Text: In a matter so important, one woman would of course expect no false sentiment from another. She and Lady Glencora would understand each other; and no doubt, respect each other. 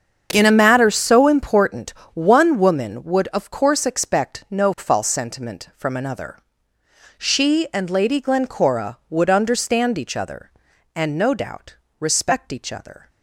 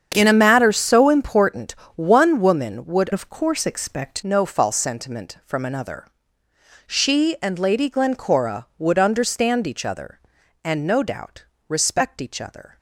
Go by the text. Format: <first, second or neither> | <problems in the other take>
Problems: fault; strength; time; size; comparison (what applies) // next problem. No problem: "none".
first | starts louder than the rest; strong; until 1.1 s; 8 dB; strong in the first // changes voice from "of" to "expect"; from 3.1 to 4.2 s; 1.1 s long